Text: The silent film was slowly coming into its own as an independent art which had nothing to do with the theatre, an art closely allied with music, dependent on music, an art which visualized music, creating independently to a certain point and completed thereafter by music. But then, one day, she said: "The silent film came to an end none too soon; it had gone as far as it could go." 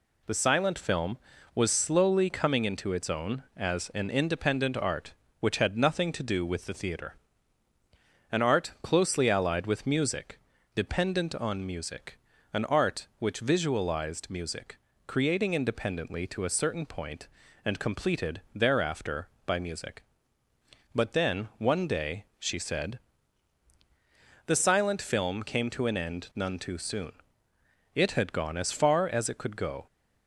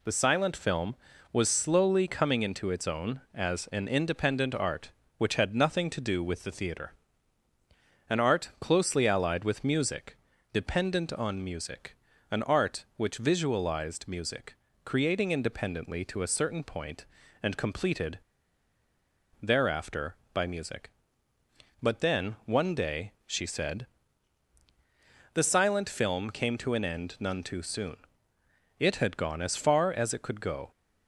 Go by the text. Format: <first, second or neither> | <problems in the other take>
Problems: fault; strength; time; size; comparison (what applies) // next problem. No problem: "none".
first | pauses between "completed" and "thereafter"; at 18.1 s; 1.2 s long